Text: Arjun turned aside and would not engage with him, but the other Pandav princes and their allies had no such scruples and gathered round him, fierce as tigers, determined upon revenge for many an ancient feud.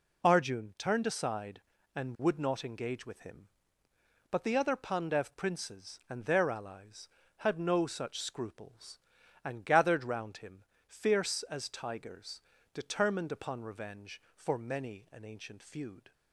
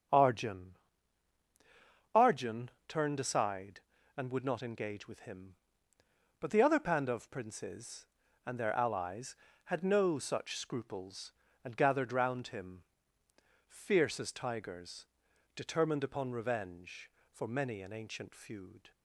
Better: first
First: none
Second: starts louder than the rest; until 2.5 s; 7 dB // says "Arjun" twice; at 2.1 s

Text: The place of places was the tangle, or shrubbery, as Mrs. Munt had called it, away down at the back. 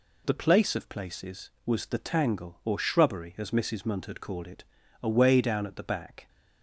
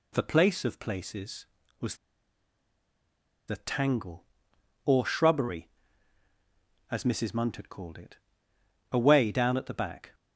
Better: first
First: none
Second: pauses between "was" and "the"; strong; at 1.9 s; 1.5 s long

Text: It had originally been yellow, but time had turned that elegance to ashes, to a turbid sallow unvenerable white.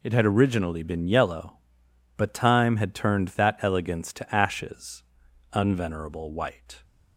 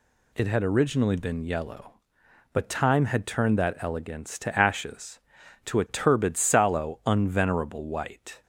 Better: second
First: skips "to a turbid sallow"; at 5.2 s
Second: none

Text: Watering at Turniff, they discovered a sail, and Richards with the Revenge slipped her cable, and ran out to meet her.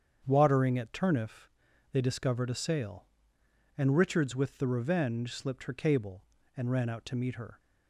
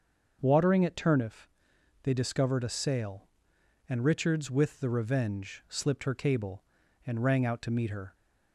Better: first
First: starts louder than the rest; strong; until 1.2 s; 7.5 dB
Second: starts louder than the rest; until 1.4 s; 6 dB // says "rang" for "ran"; at 7.2 s

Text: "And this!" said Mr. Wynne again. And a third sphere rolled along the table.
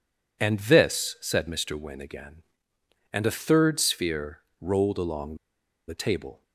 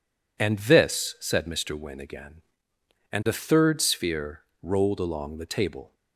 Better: second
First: pauses between "sphere" and "rolled"; slight; at 4.4 s; 0.20 s long // pauses between "along" and "the"; noticeable; at 5.3 s; 0.51 s long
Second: pauses between "sphere" and "rolled"; slight; at 4.4 s; 0.20 s long

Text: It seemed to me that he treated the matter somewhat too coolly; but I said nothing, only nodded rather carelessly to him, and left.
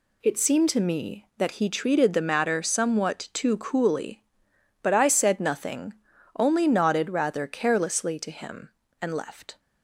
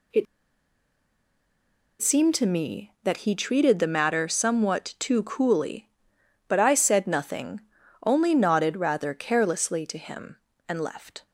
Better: first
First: none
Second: pauses between "It" and "seemed"; strong; at 0.2 s; 1.7 s long

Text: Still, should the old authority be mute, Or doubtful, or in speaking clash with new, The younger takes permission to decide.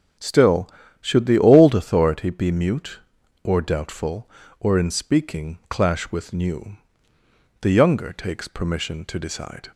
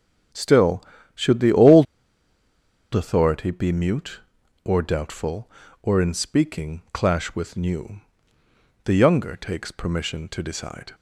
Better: first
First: starts louder than the rest; strong; until 1.5 s; 7 dB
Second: starts louder than the rest; strong; until 1.6 s; 7 dB // pauses between "old" and "authority"; at 1.8 s; 1.1 s long

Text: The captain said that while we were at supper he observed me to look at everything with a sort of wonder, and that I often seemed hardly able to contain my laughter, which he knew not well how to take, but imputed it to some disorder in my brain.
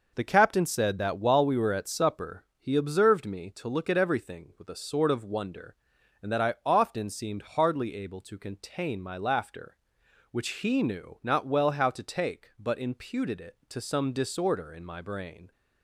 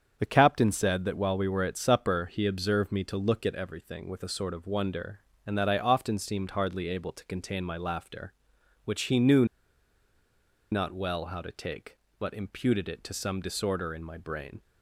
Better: first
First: none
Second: starts louder than the rest; strong; until 1.1 s; 7.5 dB // pauses between "knew" and "not"; strong; at 9.4 s; 1.2 s long

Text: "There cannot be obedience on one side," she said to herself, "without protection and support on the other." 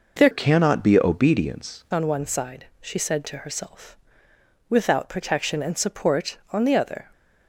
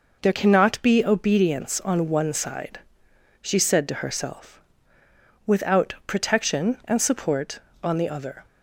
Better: second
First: changes voice from "cannot" to "obedience"; from 0.3 to 1.8 s; 1.5 s long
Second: none

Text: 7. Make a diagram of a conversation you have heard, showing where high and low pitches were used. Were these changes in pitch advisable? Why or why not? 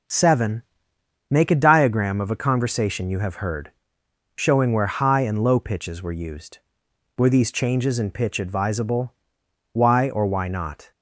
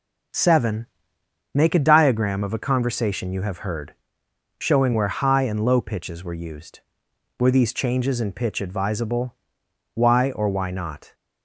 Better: neither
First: none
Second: none

